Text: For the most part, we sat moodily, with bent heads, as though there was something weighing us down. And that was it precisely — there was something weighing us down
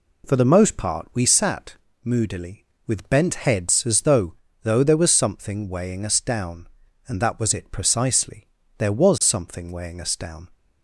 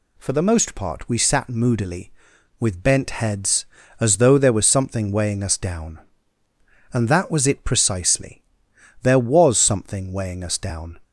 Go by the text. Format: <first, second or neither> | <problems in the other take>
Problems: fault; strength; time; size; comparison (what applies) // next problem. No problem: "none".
second | pauses between "sat" and "moodily"; slight; at 1.7 s; 0.28 s long // says "though" twice; at 4.6 s